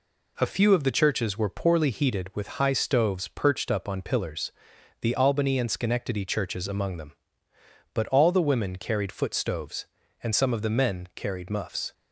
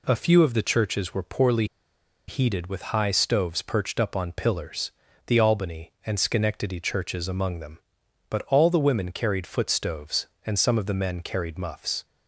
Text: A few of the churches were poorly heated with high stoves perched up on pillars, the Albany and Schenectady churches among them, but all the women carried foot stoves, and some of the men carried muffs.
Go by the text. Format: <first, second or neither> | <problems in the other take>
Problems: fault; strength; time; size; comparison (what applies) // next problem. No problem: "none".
first | pauses between "poorly" and "heated"; noticeable; at 1.6 s; 0.63 s long